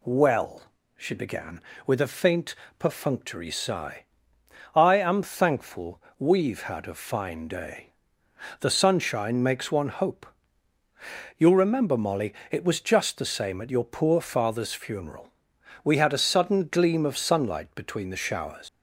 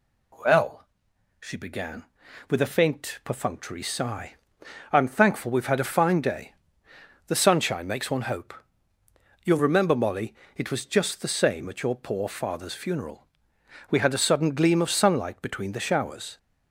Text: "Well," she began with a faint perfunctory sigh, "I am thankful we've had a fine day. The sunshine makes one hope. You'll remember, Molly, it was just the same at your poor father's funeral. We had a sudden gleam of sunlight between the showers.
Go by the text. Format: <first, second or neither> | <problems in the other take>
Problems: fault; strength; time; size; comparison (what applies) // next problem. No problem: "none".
second | pauses between "faint" and "perfunctory"; slight; at 2.5 s; 0.24 s long // pauses between "thankful" and "we've"; slight; at 6.0 s; 0.16 s long // leaves "showers" unfinished; at 18.6 s; 105 ms